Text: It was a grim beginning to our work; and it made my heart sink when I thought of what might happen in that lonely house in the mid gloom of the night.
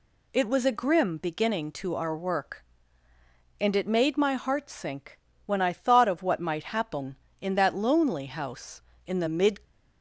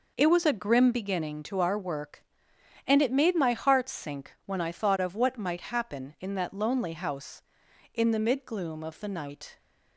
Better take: second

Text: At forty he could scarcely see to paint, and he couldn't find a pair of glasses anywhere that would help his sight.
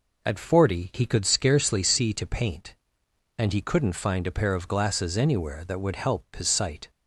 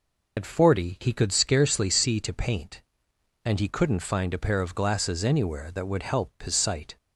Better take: first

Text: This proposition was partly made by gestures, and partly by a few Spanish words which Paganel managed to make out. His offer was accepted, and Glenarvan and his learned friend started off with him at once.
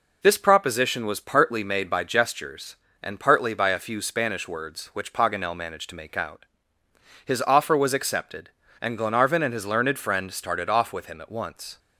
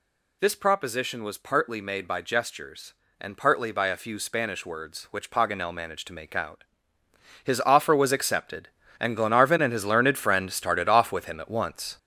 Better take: first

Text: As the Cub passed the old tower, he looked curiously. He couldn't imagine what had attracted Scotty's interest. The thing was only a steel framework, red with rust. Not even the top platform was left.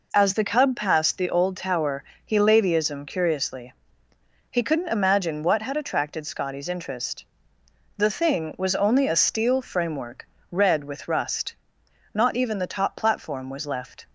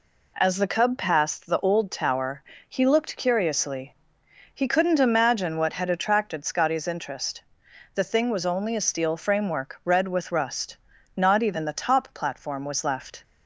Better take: second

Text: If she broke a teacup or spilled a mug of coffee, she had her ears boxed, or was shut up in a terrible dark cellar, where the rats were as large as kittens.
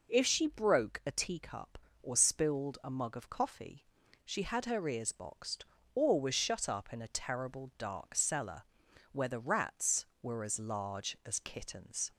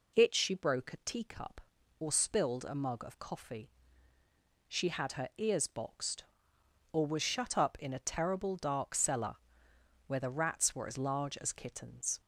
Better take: first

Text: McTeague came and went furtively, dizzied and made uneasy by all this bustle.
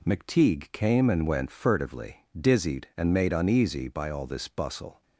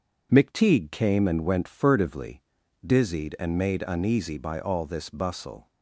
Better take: neither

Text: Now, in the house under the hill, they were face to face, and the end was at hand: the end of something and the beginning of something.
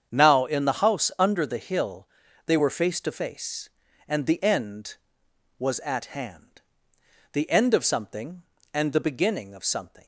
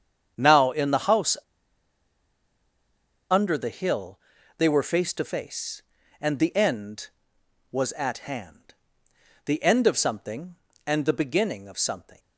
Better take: first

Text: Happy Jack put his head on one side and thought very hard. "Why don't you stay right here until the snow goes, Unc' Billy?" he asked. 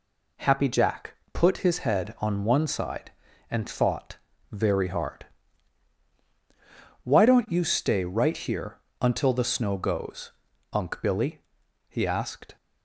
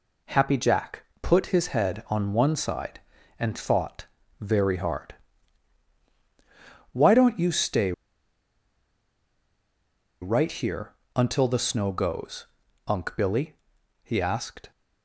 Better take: first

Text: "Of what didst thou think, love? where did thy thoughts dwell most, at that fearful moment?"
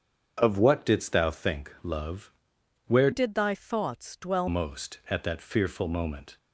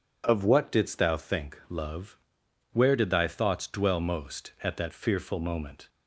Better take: second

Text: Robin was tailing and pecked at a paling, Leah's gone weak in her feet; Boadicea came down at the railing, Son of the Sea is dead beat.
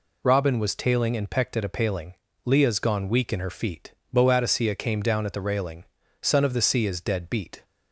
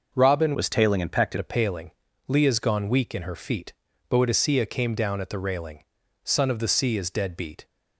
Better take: first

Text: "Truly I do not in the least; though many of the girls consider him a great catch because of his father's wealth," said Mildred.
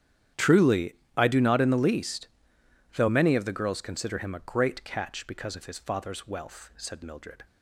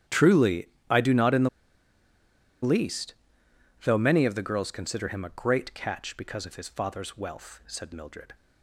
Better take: first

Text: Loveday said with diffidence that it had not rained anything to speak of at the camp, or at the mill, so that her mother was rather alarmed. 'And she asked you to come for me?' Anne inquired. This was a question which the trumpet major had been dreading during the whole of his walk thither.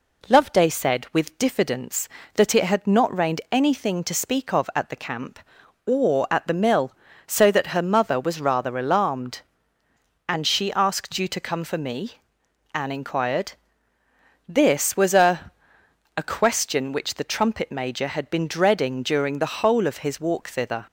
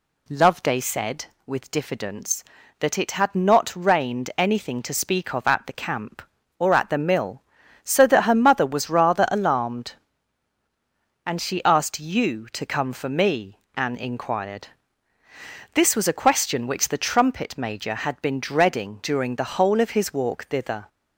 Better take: second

